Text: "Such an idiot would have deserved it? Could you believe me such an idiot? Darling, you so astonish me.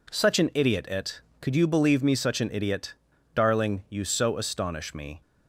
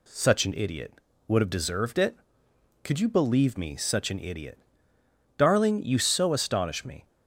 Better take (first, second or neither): second